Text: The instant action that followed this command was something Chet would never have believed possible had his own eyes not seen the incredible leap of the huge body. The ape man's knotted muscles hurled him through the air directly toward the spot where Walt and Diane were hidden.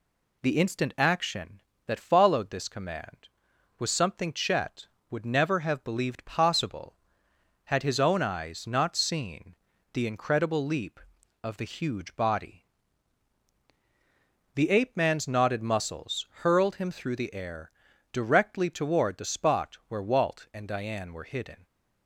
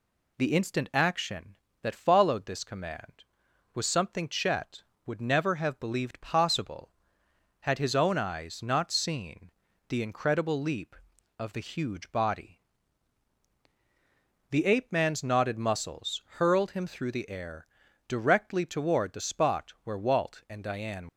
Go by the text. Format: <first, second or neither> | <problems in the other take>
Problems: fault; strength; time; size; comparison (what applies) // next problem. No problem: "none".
first | pauses between "seen" and "the"; slight; at 9.5 s; 0.36 s long; slight in the first // pauses between "air" and "directly"; at 17.6 s; 0.42 s long; also in the first // stops before "were hidden"; at 21.0 s